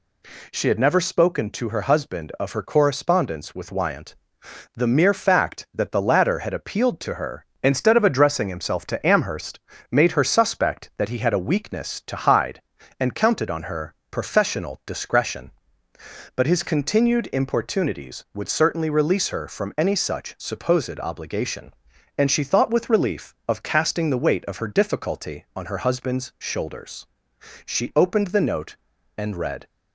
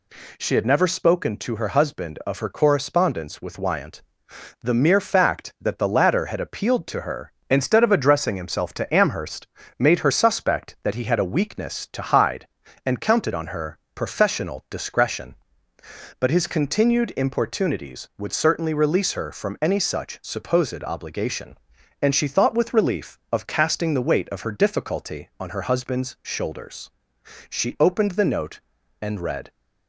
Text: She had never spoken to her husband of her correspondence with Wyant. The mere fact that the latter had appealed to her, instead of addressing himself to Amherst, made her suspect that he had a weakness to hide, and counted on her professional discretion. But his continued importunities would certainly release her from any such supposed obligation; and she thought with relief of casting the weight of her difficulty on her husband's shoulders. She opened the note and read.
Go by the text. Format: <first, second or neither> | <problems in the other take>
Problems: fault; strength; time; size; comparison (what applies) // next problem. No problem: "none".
neither | pauses between "her" and "professional"; slight; the same in both